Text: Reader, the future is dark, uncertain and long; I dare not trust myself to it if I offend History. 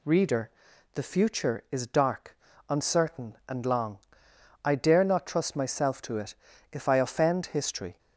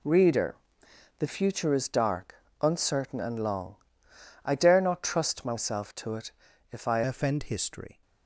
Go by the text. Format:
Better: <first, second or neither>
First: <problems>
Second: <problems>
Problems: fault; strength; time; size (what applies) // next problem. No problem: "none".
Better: first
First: pauses between "it" and "if"; at 6.3 s; 0.38 s long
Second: pauses between "it" and "if"; at 6.3 s; 0.40 s long // changes voice at "offend"; from 7.0 s on; 1.0 s long